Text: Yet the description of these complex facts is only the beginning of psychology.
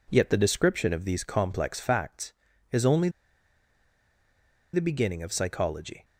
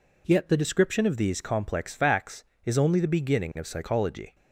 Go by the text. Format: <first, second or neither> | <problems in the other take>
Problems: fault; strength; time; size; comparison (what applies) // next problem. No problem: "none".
second | pauses between "only" and "the"; strong; at 3.0 s; 1.6 s long